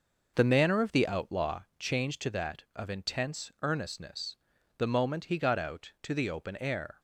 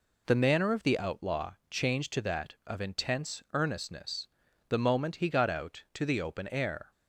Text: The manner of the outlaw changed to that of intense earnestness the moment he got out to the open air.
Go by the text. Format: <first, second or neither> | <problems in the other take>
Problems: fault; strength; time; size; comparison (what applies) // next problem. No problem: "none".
second | starts louder than the rest; noticeable; until 1.8 s; 6 dB // pauses between "outlaw" and "changed"; slight; at 1.6 s; 0.16 s long; slight in the second // pauses between "earnestness" and "the"; at 4.3 s; 0.42 s long; also in the second